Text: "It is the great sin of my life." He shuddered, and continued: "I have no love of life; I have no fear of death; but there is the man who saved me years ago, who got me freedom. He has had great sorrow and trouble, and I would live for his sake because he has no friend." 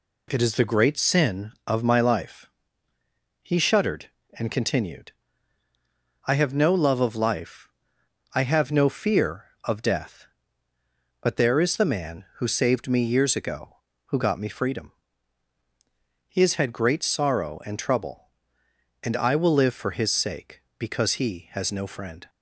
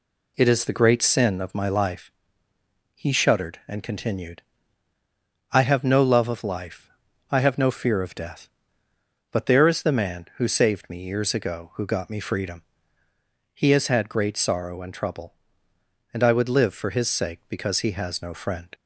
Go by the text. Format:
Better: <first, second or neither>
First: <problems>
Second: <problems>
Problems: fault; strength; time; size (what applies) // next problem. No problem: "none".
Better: second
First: says "will" for "would"; at 19.3 s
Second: none